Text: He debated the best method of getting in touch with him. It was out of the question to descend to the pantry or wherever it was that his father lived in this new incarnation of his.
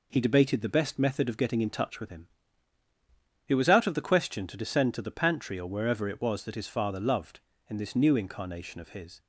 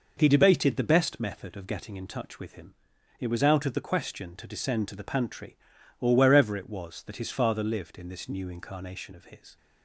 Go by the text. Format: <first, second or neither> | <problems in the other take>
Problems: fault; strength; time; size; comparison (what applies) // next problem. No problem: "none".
second | says "loved" for "lived"; at 6.9 s